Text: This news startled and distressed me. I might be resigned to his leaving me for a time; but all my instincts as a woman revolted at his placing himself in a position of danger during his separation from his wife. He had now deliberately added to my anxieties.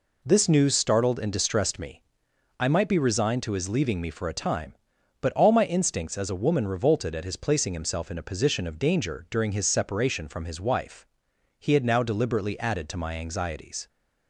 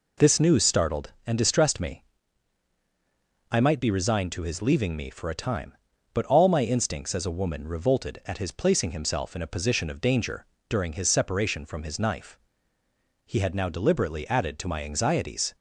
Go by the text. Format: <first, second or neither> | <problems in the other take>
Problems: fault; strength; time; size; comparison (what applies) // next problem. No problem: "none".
first | pauses between "danger" and "during"; slight; at 10.4 s; 0.24 s long // says "knife" for "wife"; at 12.0 s